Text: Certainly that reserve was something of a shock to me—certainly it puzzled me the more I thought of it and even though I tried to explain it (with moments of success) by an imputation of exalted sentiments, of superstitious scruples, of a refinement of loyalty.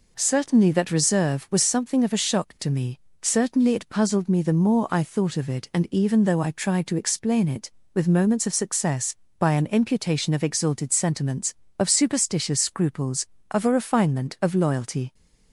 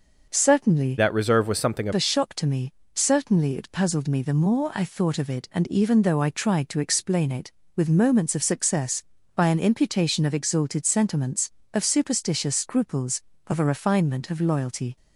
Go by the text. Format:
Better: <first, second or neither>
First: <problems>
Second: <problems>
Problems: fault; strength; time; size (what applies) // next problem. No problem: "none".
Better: first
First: none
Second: changes voice from "that" to "of"; from 0.9 to 1.9 s; 1.0 s long